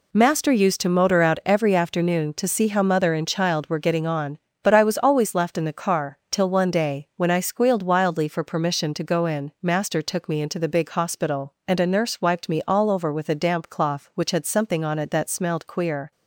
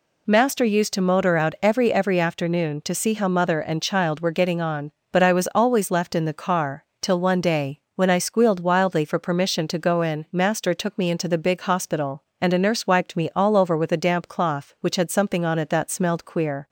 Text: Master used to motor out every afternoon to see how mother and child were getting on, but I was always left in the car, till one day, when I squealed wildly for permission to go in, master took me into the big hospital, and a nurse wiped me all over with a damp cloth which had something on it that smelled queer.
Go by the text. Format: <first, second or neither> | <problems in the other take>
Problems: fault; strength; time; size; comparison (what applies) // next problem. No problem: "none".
first | says "every" twice; at 1.9 s